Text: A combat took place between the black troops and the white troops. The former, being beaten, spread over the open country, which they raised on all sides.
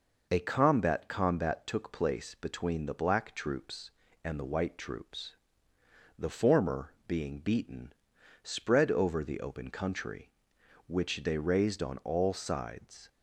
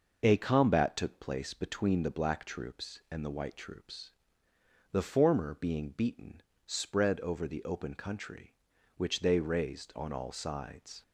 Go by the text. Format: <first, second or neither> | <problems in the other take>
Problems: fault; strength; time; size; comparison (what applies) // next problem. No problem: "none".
second | says "combat" twice; at 1.0 s